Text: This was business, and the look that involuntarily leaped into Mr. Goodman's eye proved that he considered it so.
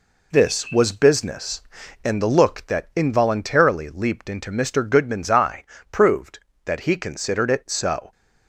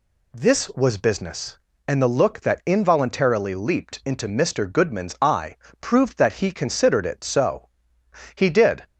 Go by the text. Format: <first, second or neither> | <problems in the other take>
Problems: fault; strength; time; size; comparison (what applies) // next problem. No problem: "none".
first | pauses between "eye" and "proved"; slight; at 5.5 s; 0.24 s long; slight in the first // goes on to say "He did"; from 8.3 s on; 0.50 s long